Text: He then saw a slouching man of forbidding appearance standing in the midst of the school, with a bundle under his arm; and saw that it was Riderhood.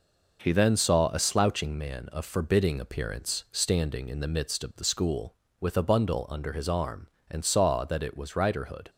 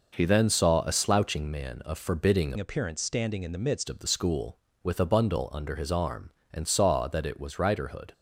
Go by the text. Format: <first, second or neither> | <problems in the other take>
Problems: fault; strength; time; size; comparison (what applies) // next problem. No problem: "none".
first | changes voice from "appearance" to "midst"; from 2.5 to 3.8 s; 1.3 s long